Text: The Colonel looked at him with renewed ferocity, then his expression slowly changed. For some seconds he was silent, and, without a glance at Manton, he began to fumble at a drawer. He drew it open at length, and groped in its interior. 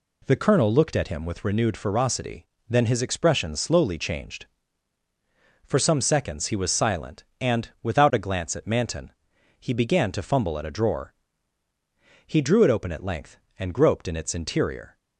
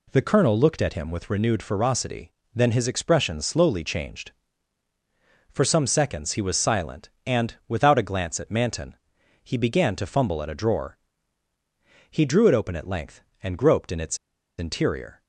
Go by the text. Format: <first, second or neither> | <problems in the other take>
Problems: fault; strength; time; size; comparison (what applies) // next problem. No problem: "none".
first | pauses between "its" and "interior"; at 14.1 s; 0.41 s long